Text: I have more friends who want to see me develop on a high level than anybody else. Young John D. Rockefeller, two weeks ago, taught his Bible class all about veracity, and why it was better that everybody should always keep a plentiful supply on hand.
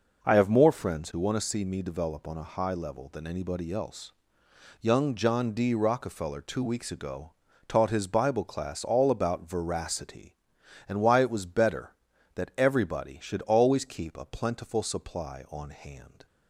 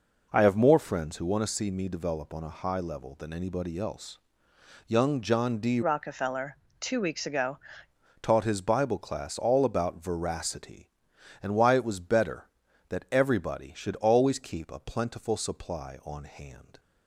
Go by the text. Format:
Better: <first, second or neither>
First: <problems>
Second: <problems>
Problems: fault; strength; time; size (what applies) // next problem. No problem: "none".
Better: first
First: none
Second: changes voice from "Rockefeller" to "ago"; from 5.8 to 7.5 s; 1.7 s long